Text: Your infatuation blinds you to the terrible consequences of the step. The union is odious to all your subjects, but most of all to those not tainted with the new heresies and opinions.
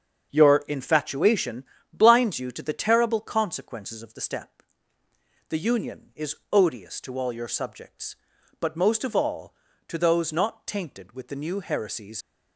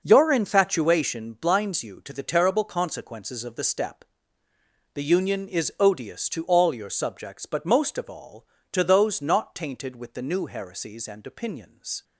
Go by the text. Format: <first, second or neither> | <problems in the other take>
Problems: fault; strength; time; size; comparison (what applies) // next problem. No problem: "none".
second | starts louder than the rest; until 1.3 s; 7 dB // pauses between "infatuation" and "blinds"; slight; at 1.6 s; 0.28 s long // pauses between "is" and "odious"; slight; at 6.3 s; 0.16 s long // stops before "and opinions"; at 12.2 s